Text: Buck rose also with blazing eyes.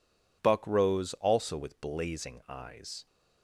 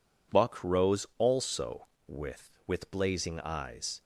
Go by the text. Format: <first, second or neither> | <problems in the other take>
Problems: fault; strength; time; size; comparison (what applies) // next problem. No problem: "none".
first | says "with" twice; at 2.6 s